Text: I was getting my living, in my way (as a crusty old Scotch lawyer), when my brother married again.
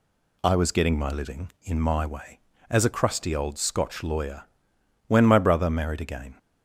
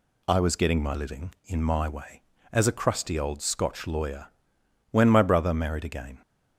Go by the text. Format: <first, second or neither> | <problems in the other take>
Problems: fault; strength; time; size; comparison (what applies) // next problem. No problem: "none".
neither | none